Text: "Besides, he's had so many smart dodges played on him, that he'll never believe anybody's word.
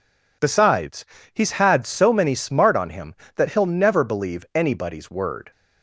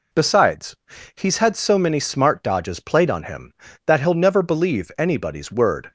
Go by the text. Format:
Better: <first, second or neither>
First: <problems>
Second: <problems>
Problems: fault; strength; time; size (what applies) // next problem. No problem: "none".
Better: second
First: skips "dodges played"; at 2.7 s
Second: none